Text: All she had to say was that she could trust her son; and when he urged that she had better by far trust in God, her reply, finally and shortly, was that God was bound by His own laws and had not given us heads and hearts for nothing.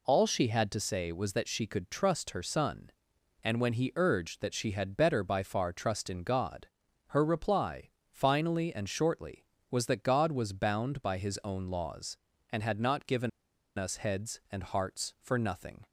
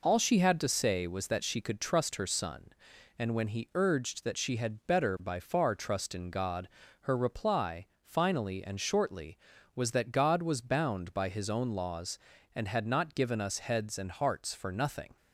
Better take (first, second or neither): second